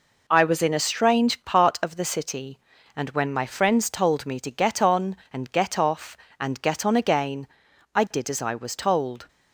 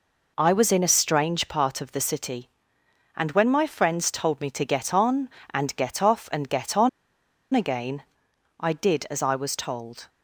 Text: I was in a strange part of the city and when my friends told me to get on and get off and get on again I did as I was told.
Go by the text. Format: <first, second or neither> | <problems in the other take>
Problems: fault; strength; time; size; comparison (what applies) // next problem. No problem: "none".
first | pauses between "on" and "again"; noticeable; at 6.8 s; 0.64 s long // pauses between "again" and "I"; noticeable; at 8.0 s; 0.56 s long; noticeable in the first